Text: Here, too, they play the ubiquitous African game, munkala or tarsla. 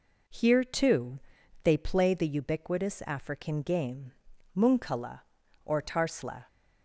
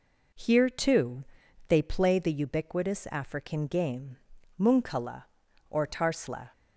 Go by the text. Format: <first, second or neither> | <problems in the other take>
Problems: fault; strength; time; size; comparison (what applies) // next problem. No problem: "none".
neither | none